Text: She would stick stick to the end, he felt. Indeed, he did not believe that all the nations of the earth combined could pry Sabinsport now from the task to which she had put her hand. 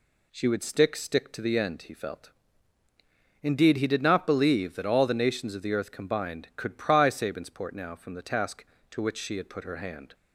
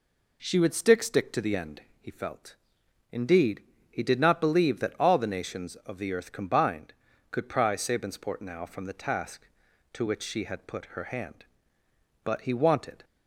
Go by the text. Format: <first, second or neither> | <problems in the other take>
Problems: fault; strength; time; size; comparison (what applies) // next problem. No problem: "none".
first | goes on to say "But he wanted"; noticeable; from 12.2 s on; 0.80 s long